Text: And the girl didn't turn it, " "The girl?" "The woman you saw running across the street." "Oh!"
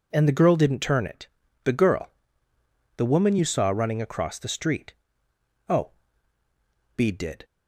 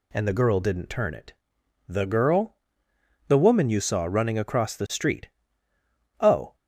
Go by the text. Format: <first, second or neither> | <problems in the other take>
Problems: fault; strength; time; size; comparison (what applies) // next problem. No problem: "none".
second | goes on to say "Bede did"; slight; from 6.9 s on; 0.48 s long